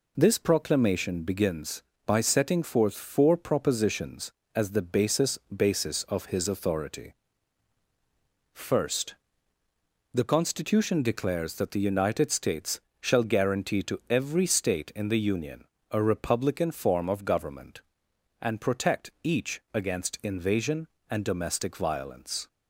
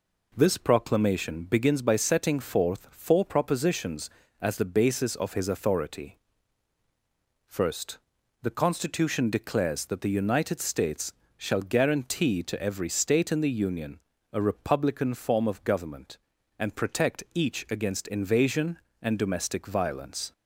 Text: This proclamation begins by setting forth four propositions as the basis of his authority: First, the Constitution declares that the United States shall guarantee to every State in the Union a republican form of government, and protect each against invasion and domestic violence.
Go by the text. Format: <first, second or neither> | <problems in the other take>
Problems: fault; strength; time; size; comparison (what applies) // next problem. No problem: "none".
second | says "basis" twice; at 5.5 s // pauses between "States" and "shall"; slight; at 12.7 s; 0.22 s long; slight in the second // pauses between "Union" and "a"; slight; at 15.6 s; 0.26 s long; slight in the second